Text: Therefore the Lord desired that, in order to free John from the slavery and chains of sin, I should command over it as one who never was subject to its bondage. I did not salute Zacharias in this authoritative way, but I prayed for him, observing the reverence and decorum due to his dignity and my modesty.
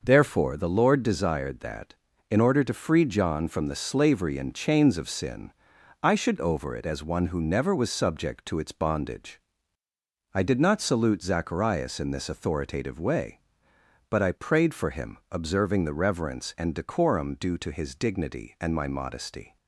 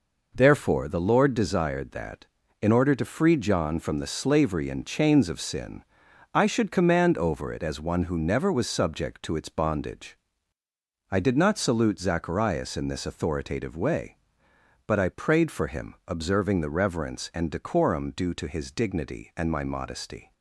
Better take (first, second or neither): second